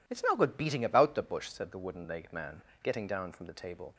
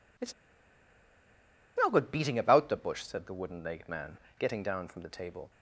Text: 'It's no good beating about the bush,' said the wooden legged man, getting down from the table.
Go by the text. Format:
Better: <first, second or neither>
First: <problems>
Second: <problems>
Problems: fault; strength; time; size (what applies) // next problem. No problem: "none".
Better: first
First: none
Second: pauses between "It's" and "no"; strong; at 0.3 s; 1.4 s long